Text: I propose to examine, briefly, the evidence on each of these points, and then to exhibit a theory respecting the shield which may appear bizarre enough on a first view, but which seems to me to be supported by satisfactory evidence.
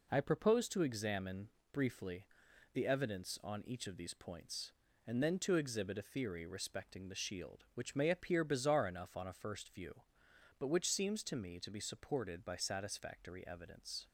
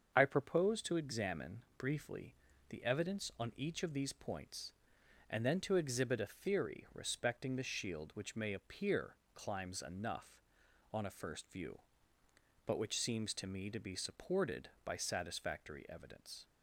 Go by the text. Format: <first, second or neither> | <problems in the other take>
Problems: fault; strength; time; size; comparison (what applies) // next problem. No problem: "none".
first | starts louder than the rest; until 1.1 s; 7 dB // says "climbs" for "bizarre"; at 9.3 s